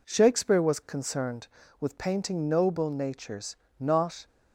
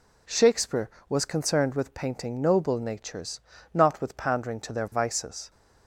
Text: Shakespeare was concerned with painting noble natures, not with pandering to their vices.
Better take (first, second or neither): second